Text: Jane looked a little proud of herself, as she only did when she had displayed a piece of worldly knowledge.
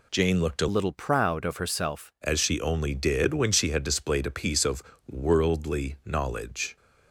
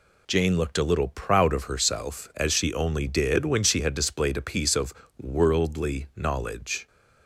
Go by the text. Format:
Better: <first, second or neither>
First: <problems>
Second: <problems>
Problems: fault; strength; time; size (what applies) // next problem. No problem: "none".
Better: second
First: changes voice from "little" to "herself"; from 0.7 to 2.1 s; 1.4 s long // pauses between "of" and "worldly"; slight; at 4.8 s; 0.28 s long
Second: pauses between "of" and "worldly"; slight; at 4.9 s; 0.28 s long